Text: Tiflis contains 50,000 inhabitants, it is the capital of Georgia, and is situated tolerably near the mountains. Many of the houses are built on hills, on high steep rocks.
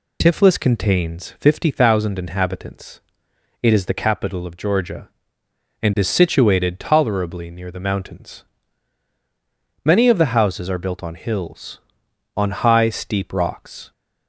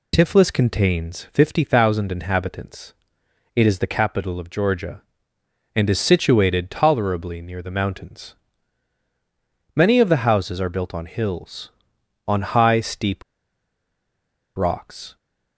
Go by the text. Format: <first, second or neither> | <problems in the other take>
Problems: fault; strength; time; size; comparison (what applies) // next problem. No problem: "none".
first | pauses between "steep" and "rocks"; strong; at 13.2 s; 1.3 s long